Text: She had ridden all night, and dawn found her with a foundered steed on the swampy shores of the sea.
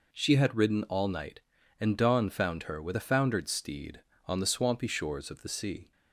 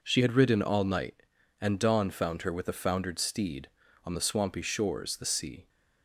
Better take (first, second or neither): first